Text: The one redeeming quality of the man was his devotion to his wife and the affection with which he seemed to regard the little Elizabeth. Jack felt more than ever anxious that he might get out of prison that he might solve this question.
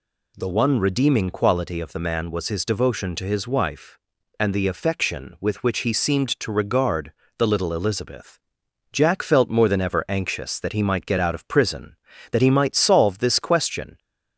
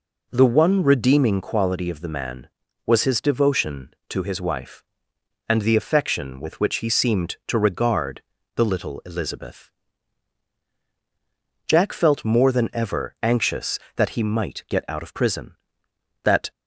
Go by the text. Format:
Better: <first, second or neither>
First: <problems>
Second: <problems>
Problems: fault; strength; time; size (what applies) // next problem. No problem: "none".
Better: first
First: pauses between "regard" and "the"; slight; at 7.1 s; 0.26 s long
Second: pauses between "regard" and "the"; slight; at 8.2 s; 0.34 s long // stops before "he might solve this question"; at 16.5 s